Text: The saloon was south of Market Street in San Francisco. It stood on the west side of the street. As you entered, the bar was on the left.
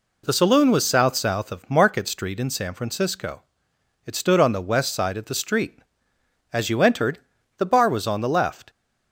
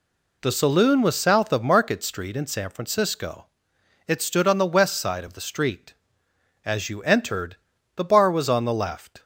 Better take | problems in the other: second | says "south" twice; at 1.1 s

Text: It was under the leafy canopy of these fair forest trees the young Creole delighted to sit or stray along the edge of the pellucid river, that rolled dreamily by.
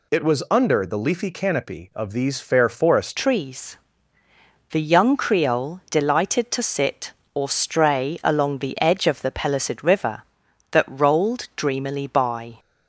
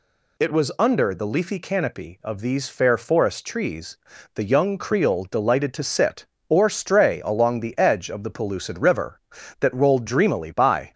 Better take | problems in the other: second | changes voice at "trees"; from 3.1 s on; 9.4 s long // pauses between "trees" and "the"; noticeable; at 3.7 s; 0.96 s long; also in the second

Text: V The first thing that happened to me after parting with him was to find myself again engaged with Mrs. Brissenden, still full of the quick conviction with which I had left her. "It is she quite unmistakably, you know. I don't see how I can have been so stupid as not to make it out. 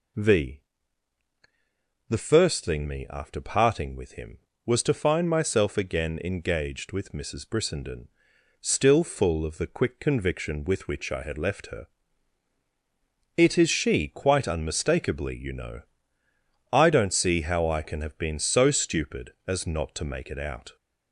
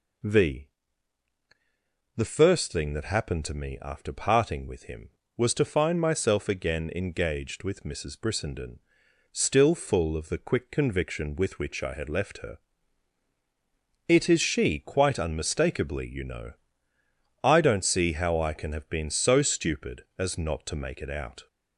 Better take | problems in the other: second | pauses between "V" and "The"; strong; at 0.5 s; 1.5 s long; strong in the second // skips "that happened to"; at 2.8 s

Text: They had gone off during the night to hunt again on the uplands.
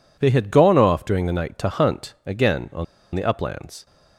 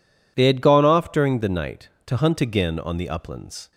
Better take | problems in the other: second | pauses between "on" and "the"; slight; at 2.8 s; 0.30 s long

